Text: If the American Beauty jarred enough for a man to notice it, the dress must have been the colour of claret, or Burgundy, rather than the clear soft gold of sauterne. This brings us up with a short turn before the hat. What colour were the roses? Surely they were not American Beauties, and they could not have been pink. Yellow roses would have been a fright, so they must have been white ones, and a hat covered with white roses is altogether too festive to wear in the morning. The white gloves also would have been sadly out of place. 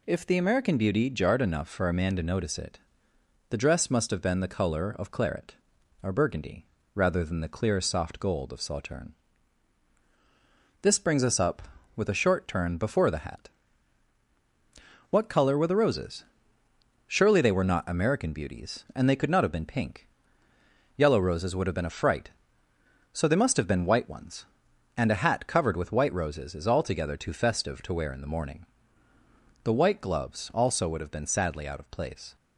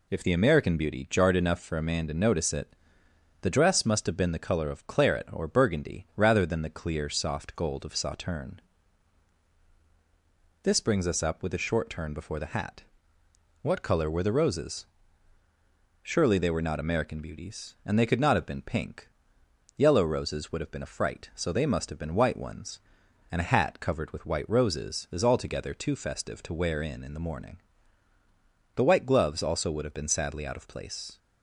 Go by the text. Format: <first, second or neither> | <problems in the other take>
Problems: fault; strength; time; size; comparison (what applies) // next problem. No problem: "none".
first | says "in" twice; at 27.0 s